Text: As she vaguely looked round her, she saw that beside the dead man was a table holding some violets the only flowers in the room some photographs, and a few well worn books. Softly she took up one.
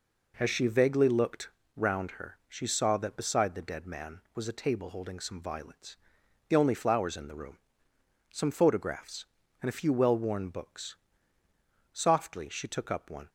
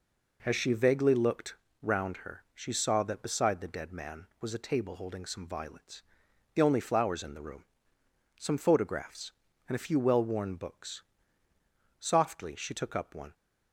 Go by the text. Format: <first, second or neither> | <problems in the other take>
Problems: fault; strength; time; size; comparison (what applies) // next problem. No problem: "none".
neither | pauses between "looked" and "round"; slight; the same in both // pauses between "violets" and "the"; noticeable; the same in both // pauses between "room" and "some"; noticeable; the same in both